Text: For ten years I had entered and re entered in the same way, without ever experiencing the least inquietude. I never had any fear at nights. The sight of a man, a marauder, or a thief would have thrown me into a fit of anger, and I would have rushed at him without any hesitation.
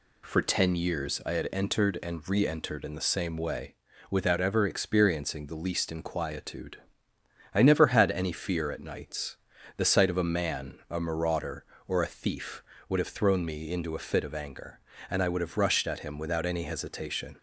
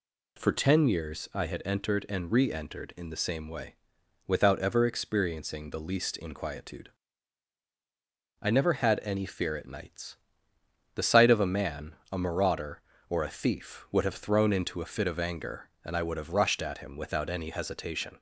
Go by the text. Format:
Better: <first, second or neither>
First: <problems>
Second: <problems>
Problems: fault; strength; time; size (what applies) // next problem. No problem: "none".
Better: first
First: none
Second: skips "me"; at 14.5 s